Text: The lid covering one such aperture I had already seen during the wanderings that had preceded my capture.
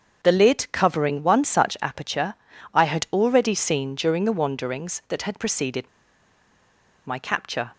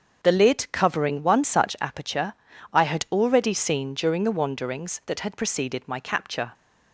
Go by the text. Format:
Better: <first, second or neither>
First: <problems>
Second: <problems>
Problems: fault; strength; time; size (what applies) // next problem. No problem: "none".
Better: second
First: starts louder than the rest; until 1.2 s; 7 dB // pauses between "aperture" and "I"; at 2.3 s; 0.40 s long // pauses between "preceded" and "my"; at 5.8 s; 1.1 s long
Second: starts louder than the rest; until 1.2 s; 7 dB // pauses between "aperture" and "I"; at 2.3 s; 0.40 s long